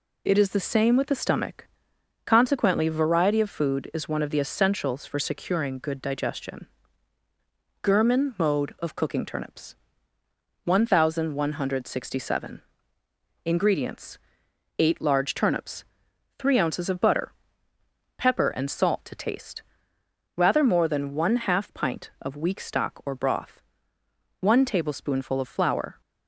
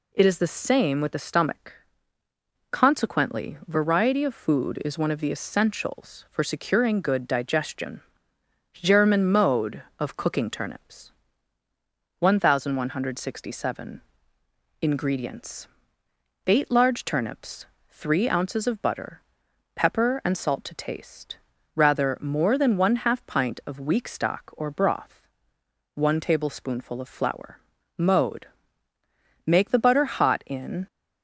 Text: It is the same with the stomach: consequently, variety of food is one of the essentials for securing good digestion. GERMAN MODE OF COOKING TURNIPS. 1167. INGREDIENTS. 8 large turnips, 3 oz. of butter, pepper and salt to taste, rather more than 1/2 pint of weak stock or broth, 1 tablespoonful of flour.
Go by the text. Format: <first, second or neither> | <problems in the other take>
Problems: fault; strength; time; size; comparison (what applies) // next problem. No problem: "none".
first | goes on to say "Mode Make the butter hot in"; strong; from 27.9 s on; 2.9 s long